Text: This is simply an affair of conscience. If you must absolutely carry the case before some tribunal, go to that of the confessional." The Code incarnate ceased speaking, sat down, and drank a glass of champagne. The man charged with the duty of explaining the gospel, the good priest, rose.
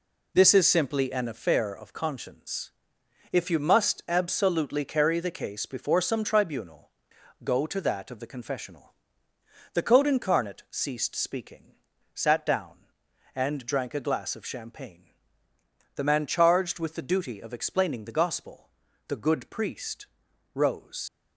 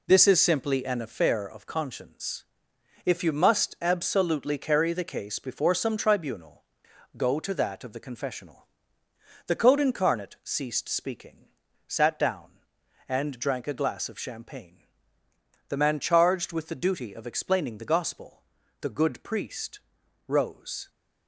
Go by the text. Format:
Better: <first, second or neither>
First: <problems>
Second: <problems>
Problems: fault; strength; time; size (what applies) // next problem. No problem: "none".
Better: second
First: leaves "rose" unfinished; at 21.0 s; 85 ms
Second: none